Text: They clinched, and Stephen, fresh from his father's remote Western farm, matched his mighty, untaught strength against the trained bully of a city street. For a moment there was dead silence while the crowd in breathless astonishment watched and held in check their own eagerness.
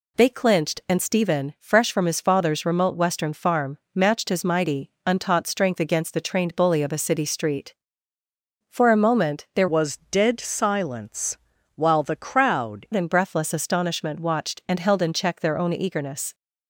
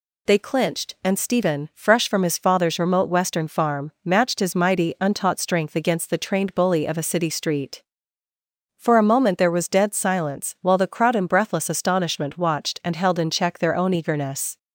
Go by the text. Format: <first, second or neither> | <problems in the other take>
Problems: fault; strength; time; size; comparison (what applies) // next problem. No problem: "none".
second | changes voice from "was" to "crowd"; from 9.6 to 12.8 s; 3.2 s long // pauses between "silence" and "while"; at 11.3 s; 0.38 s long